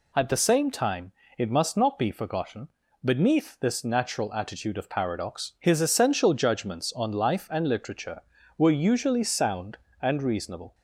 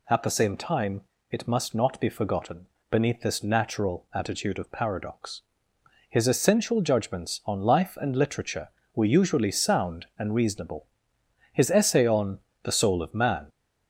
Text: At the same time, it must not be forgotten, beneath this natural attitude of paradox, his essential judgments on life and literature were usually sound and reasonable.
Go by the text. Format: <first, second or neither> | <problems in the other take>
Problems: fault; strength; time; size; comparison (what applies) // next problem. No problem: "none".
first | goes on to say "His essay on The Soul of Man"; strong; from 11.5 s on; 1.9 s long